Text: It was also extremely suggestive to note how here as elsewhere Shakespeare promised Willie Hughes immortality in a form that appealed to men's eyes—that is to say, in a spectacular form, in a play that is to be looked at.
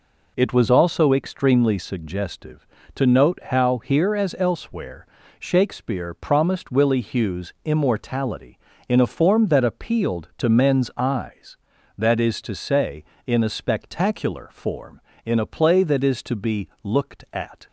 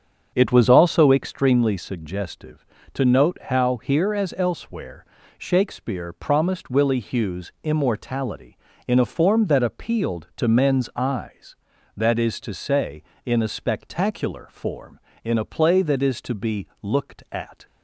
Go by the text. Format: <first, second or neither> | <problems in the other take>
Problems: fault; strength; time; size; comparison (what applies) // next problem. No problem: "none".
first | starts louder than the rest; strong; until 1.5 s; 7.5 dB // pauses between "elsewhere" and "Shakespeare"; slight; at 5.0 s; 0.32 s long; slight in the first